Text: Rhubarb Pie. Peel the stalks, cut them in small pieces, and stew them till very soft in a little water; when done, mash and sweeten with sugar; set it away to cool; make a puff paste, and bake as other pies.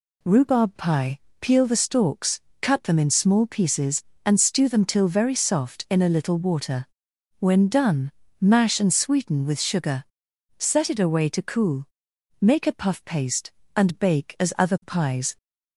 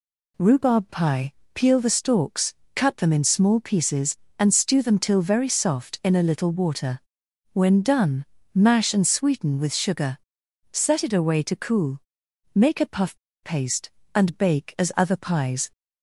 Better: first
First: none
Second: pauses between "puff" and "paste"; slight; at 13.1 s; 0.27 s long

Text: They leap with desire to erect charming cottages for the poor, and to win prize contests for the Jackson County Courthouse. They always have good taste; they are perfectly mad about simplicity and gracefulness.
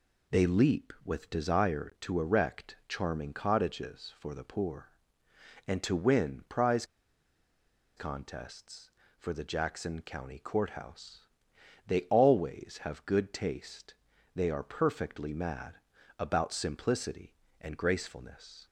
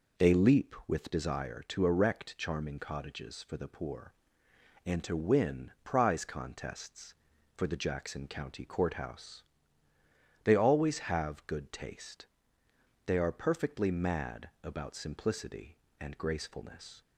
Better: second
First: pauses between "prize" and "contests"; at 6.8 s; 1.1 s long // pauses between "mad" and "about"; at 15.7 s; 0.42 s long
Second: none

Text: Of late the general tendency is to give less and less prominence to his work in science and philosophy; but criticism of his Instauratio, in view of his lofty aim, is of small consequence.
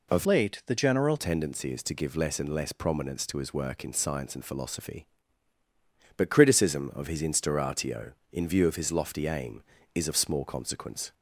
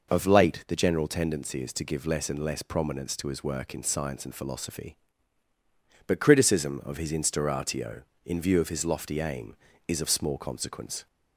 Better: second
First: changes voice from "late" to "general"; from 0.2 to 1.1 s; 0.9 s long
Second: none

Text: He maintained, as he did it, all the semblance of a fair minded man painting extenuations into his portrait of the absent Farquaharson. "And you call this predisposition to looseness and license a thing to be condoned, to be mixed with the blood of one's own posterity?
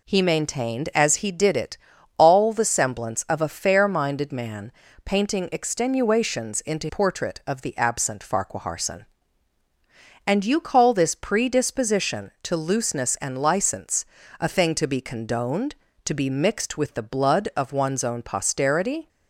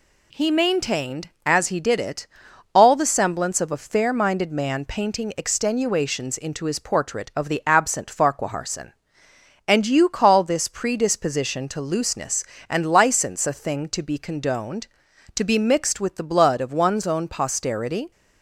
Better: second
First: pauses between "man" and "painting"; slight; at 4.6 s; 0.34 s long // skips "his"; at 6.8 s // pauses between "license" and "a"; slight; at 14.0 s; 0.34 s long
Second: none

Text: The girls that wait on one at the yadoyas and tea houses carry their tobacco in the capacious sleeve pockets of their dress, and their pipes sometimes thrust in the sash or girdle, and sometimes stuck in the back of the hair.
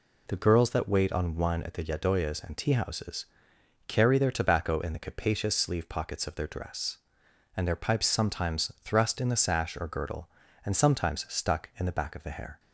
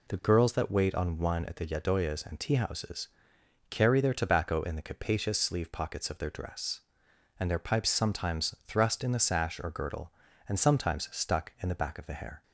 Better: neither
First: pauses between "houses" and "carry"; noticeable; at 3.2 s; 0.60 s long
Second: pauses between "houses" and "carry"; noticeable; at 3.0 s; 0.60 s long

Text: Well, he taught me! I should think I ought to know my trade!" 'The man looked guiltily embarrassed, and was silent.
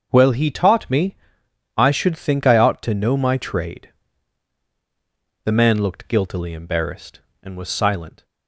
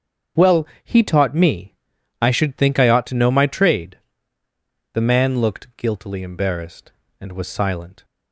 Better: neither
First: starts louder than the rest; until 1.1 s; 6.5 dB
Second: starts louder than the rest; strong; until 1.5 s; 7.5 dB

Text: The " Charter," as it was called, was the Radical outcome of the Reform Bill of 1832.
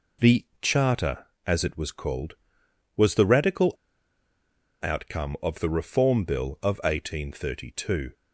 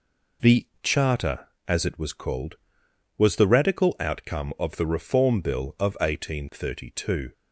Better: second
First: pauses between "Radical" and "outcome"; at 3.7 s; 1.1 s long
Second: none

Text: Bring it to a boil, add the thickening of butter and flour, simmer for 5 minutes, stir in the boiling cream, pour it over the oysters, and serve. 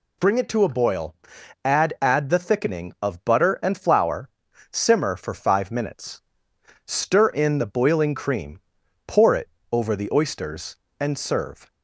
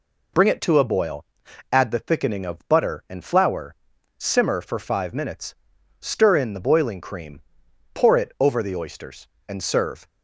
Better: second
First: says "add" twice; at 2.0 s // pauses between "it" and "over"; slight; at 9.4 s; 0.24 s long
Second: none

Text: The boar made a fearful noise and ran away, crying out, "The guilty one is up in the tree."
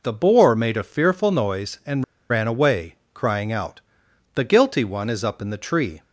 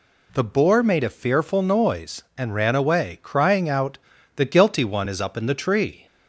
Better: second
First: pauses between "and" and "ran"; slight; at 2.0 s; 0.27 s long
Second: none

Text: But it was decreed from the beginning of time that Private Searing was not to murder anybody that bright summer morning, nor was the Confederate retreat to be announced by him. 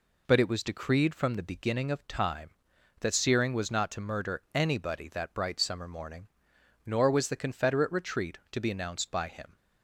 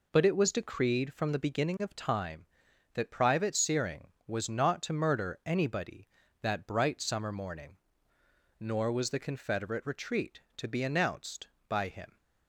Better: second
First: skips "Private"; at 3.1 s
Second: none

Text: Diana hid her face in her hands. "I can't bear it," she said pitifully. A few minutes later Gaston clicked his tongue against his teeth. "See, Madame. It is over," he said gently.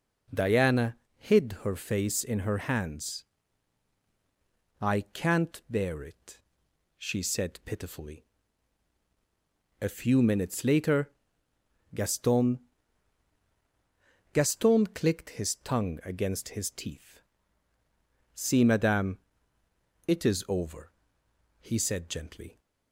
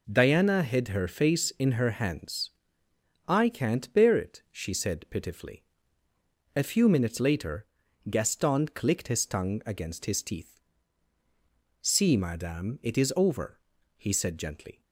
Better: second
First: pauses between "Diana" and "hid"; slight; at 0.9 s; 0.20 s long // pauses between "later" and "Gaston"; noticeable; at 11.1 s; 0.82 s long // says "Gaston" twice; at 14.3 s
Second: pauses between "later" and "Gaston"; noticeable; at 7.6 s; 0.46 s long

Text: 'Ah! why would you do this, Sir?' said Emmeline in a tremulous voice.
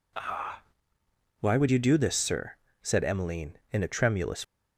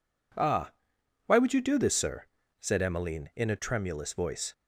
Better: second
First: stops before "voice"; at 4.4 s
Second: none

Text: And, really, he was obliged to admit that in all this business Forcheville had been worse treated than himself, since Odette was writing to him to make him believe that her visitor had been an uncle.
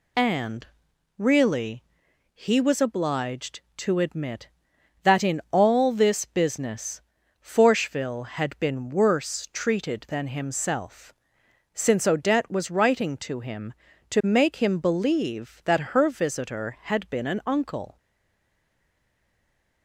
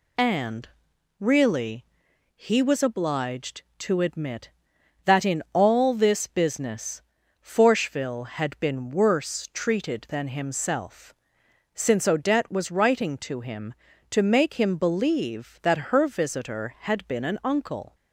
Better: second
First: pauses between "business" and "Forcheville"; at 6.9 s; 0.42 s long // stays silent after the last word; noticeable; from 17.9 s on; 1.9 s long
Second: pauses between "business" and "Forcheville"; at 7.0 s; 0.42 s long

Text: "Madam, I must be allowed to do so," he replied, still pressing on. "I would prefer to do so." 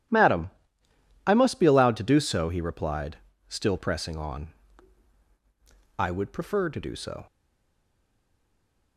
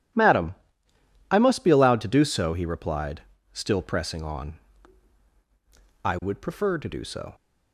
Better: second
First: stays silent after the last word; noticeable; from 7.2 s on; 1.7 s long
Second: none

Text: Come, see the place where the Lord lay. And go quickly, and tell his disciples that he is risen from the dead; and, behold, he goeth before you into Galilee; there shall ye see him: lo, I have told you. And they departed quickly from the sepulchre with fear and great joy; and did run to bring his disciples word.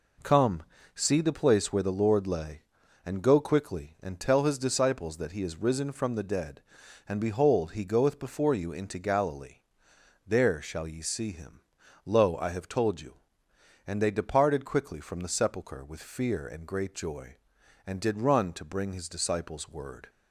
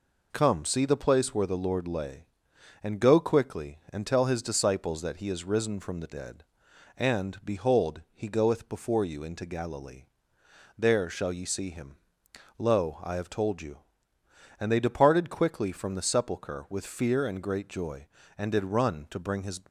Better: first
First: none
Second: stops before "disciples word"; at 19.6 s

